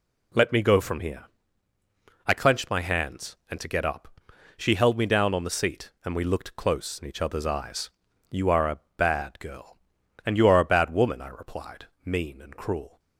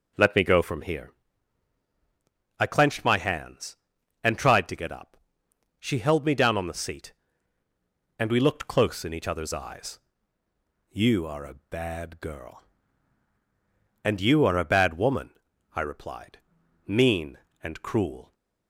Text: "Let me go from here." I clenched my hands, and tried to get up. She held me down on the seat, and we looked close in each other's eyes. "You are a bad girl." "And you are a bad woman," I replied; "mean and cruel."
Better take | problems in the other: second | skips "tried"; at 3.6 s // pauses between "a" and "bad"; slight; at 8.7 s; 0.18 s long

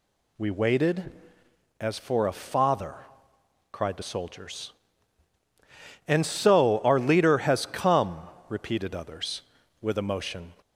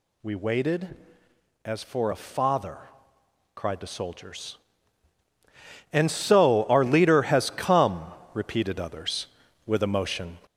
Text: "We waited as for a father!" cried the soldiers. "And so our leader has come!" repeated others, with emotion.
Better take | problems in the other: first | gets louder; noticeable; throughout; 5.5 dB

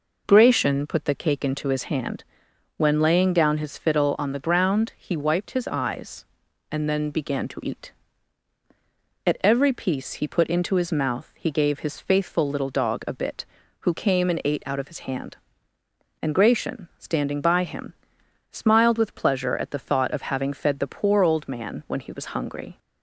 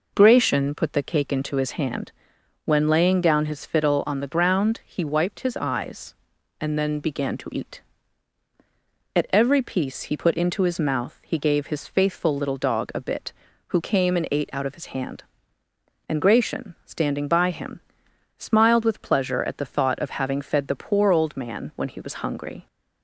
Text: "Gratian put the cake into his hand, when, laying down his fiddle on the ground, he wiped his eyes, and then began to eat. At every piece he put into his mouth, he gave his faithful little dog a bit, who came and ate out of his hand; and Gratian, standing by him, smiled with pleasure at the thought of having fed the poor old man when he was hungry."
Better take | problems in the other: neither | none

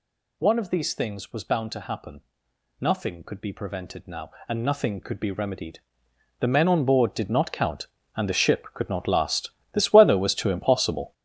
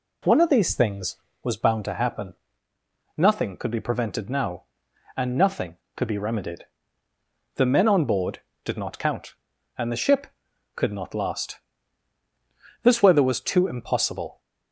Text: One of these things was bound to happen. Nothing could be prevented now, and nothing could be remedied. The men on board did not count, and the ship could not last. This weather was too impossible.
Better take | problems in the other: second | gets louder; strong; throughout; 10.5 dB

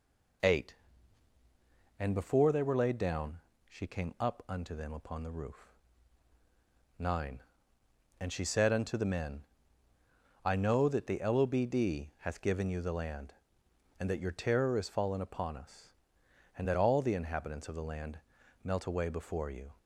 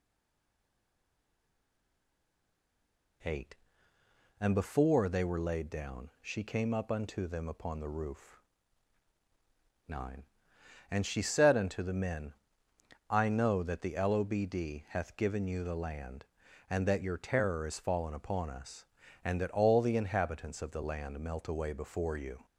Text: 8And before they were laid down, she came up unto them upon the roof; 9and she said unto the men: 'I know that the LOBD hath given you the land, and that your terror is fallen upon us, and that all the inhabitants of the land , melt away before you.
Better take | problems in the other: first | stays silent before the first word; strong; until 3.2 s; 3.2 s long

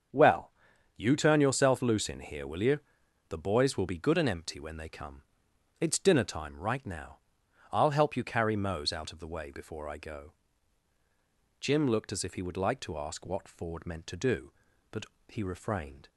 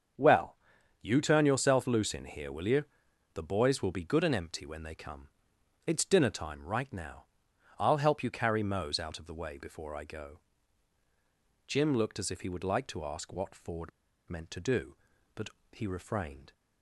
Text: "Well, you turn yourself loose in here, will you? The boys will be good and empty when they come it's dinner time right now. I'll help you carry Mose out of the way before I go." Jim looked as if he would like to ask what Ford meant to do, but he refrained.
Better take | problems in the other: first | starts louder than the rest; until 1.6 s; 7 dB; also in the first // pauses between "come" and "it's"; noticeable; at 5.2 s; 0.58 s long; noticeable in the first // pauses between "Ford" and "meant"; at 13.9 s; 0.37 s long // pauses between "but" and "he"; slight; at 15.4 s; 0.22 s long; slight in the first

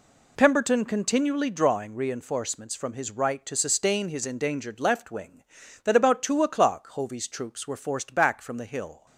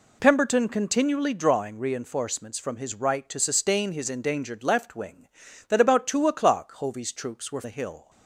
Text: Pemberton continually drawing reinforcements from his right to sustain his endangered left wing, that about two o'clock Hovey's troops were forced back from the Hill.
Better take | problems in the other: first | skips "forced back from"; at 7.6 s

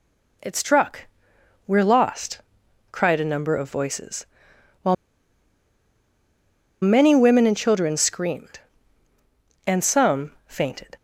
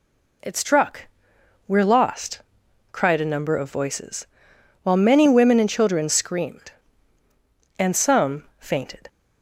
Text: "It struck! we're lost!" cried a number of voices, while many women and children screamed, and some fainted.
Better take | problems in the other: second | pauses between "while" and "many"; strong; at 4.9 s; 1.8 s long // pauses between "some" and "fainted"; slight; at 10.3 s; 0.16 s long; slight in the second

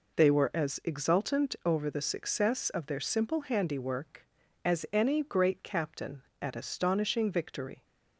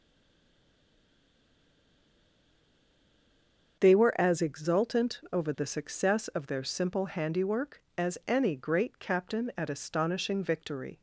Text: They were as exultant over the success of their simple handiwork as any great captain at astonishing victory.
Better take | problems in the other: first | stays silent before the first word; strong; until 3.7 s; 3.7 s long // starts louder than the rest; until 4.8 s; 6.5 dB

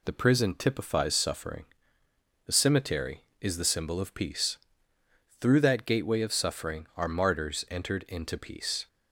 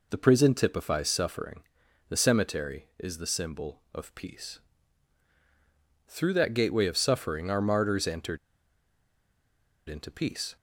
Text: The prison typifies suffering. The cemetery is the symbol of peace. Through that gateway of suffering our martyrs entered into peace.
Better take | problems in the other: first | pauses between "entered" and "into"; strong; at 8.3 s; 1.5 s long

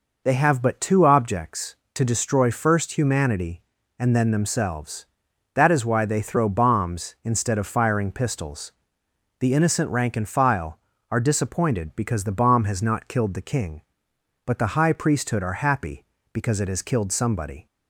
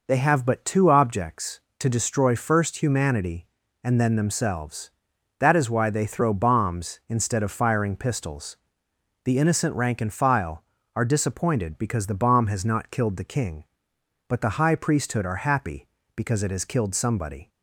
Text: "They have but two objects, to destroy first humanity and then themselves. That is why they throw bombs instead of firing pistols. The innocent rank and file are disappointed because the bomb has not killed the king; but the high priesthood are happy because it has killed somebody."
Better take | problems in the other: neither | none

